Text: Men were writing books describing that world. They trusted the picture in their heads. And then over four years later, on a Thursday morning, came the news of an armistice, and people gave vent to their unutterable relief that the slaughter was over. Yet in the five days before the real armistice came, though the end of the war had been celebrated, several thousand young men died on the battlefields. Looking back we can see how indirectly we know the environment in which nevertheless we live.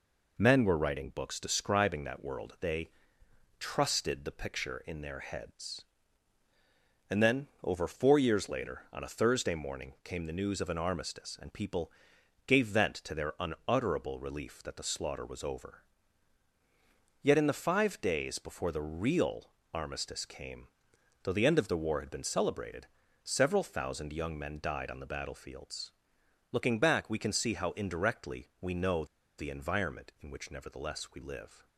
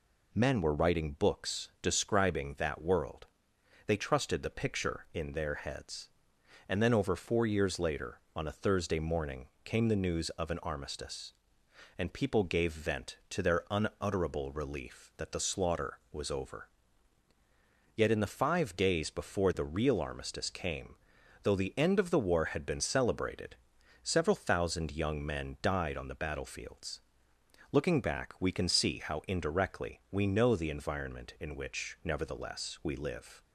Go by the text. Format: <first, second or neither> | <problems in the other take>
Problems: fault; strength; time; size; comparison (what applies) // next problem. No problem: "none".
second | pauses between "They" and "trusted"; noticeable; at 2.9 s; 0.68 s long // pauses between "then" and "over"; slight; at 7.4 s; 0.18 s long // pauses between "people" and "gave"; noticeable; at 11.9 s; 0.56 s long // pauses between "real" and "armistice"; slight; at 19.5 s; 0.22 s long // pauses between "know" and "the"; slight; at 29.0 s; 0.33 s long